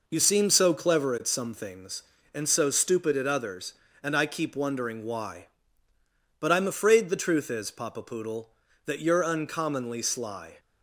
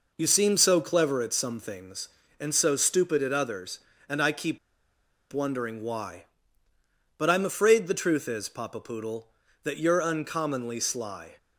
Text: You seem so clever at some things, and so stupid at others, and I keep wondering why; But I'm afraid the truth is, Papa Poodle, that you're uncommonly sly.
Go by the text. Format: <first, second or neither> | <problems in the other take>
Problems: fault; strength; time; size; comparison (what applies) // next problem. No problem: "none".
first | pauses between "keep" and "wondering"; noticeable; at 4.5 s; 0.74 s long